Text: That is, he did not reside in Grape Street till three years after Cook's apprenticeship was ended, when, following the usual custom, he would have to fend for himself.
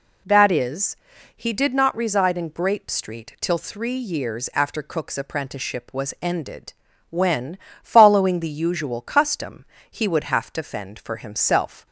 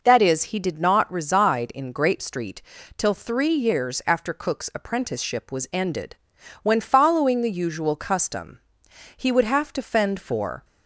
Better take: first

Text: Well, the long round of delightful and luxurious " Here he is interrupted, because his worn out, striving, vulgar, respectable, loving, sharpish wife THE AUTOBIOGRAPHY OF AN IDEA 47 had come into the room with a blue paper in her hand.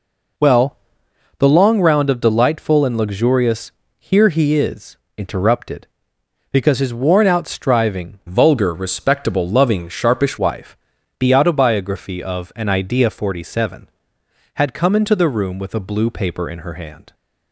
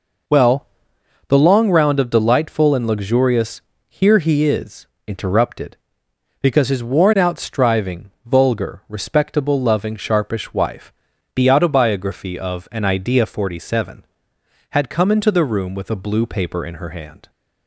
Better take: second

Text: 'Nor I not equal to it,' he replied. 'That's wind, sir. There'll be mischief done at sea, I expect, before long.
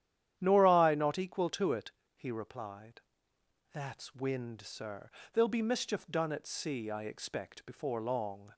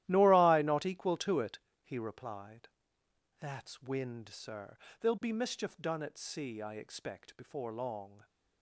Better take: first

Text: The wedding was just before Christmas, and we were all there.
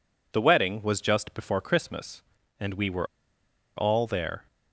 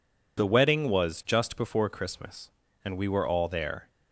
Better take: second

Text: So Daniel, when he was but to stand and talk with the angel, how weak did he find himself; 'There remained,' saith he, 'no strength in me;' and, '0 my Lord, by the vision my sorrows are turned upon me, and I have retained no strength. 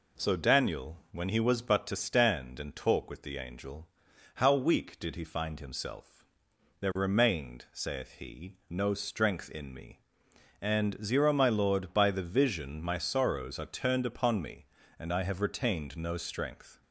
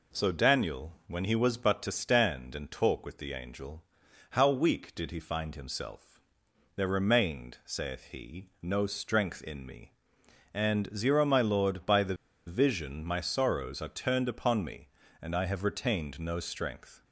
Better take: first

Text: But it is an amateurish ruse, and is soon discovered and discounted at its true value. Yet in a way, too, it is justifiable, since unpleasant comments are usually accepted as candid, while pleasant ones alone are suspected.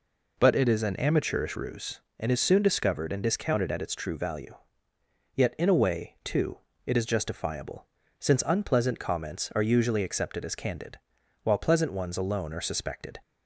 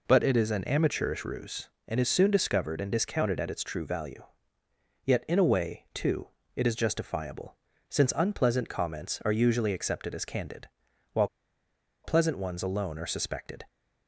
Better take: first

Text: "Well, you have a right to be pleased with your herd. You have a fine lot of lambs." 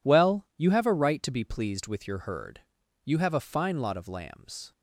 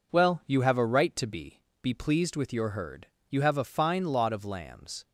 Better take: first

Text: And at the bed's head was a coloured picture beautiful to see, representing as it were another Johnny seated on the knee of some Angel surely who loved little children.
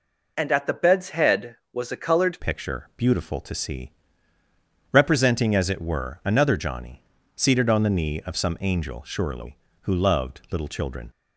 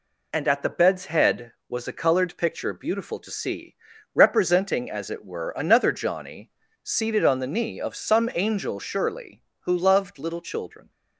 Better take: second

